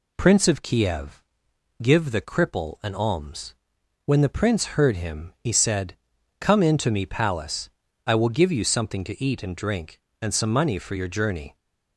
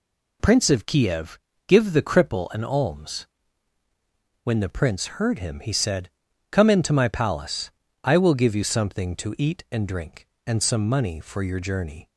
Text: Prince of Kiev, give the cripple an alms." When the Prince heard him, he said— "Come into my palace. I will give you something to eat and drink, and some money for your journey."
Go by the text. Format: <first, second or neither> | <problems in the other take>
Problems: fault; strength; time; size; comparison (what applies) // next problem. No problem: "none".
second | says "me" for "my"; at 6.9 s